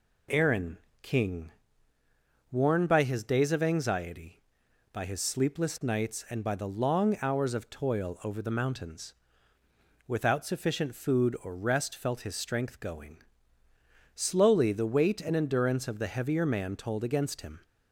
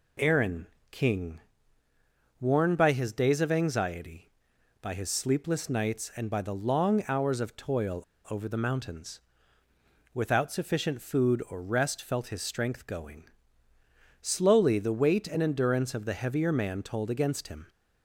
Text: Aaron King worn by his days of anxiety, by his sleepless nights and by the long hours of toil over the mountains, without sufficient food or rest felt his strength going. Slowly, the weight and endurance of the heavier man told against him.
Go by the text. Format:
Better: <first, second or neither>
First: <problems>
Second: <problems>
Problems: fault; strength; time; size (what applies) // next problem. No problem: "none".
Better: first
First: pauses between "Aaron" and "King"; slight; at 0.7 s; 0.24 s long // pauses between "King" and "worn"; at 1.4 s; 1.0 s long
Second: pauses between "Aaron" and "King"; slight; at 0.6 s; 0.24 s long // pauses between "King" and "worn"; at 1.3 s; 1.0 s long // pauses between "toil" and "over"; slight; at 8.0 s; 0.26 s long